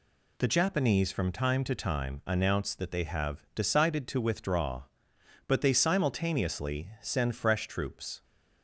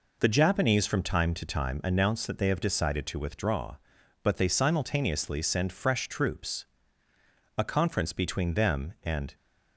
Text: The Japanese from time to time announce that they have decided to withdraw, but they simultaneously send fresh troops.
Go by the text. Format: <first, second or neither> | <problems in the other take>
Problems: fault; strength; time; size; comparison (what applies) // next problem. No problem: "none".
first | goes on to say "A conference between them and"; strong; from 7.5 s on; 1.8 s long